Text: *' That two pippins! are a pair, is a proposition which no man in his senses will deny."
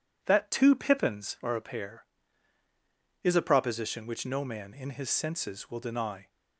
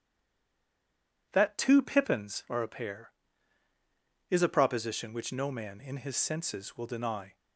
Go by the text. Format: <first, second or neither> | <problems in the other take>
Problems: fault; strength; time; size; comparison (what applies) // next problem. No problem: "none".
first | stays silent before the first word; noticeable; until 1.2 s; 1.2 s long